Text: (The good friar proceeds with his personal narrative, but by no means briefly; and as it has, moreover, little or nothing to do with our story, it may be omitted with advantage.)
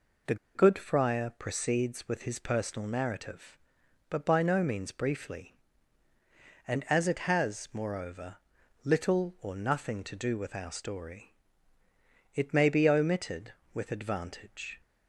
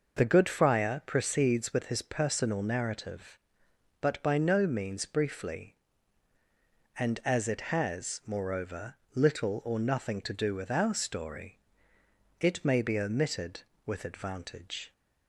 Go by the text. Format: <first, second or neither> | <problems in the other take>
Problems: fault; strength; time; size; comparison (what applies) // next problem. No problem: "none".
second | pauses between "The" and "good"; slight; at 0.3 s; 0.19 s long